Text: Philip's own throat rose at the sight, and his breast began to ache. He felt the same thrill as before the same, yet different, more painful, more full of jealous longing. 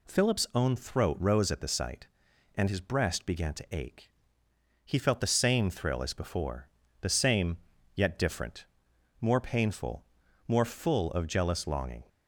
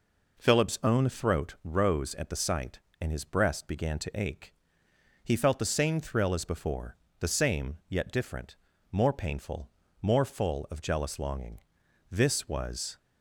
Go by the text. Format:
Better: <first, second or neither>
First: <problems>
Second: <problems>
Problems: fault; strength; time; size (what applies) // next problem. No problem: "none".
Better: first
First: pauses between "before" and "the"; slight; at 6.6 s; 0.32 s long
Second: pauses between "before" and "the"; slight; at 6.9 s; 0.24 s long // goes on to say "This was"; noticeable; from 12.1 s on; 0.86 s long